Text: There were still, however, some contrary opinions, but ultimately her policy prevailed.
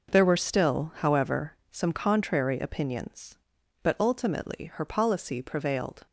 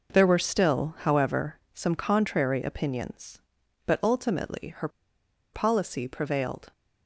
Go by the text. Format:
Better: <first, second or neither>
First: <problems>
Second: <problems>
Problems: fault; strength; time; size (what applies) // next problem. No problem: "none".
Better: first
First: none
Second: pauses between "her" and "policy"; noticeable; at 4.8 s; 0.64 s long